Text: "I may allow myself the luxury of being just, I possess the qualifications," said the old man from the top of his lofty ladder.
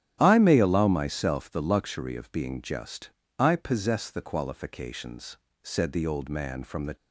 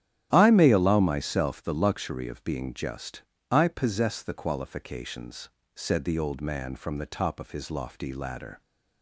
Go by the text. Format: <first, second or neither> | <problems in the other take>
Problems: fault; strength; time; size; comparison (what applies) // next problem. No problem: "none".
second | starts louder than the rest; strong; until 1.2 s; 11.5 dB; strong in the second // stops before "top of his lofty ladder"; at 6.9 s